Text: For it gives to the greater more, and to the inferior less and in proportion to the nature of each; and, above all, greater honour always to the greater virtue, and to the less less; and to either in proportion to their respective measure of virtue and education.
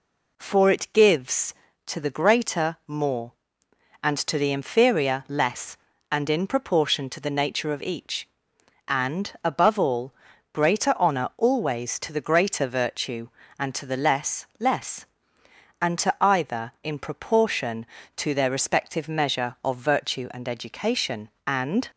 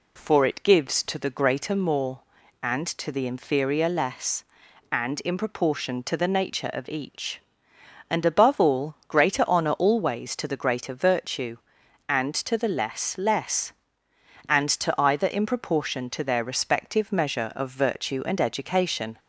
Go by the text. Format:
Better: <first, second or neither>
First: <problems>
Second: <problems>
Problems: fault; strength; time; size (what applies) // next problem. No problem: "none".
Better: second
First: goes on to say "And"; slight; from 21.4 s on; 0.42 s long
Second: none